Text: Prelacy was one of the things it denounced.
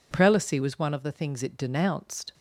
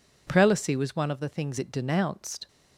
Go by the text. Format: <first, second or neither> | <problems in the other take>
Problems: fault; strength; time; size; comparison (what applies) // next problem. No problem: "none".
neither | none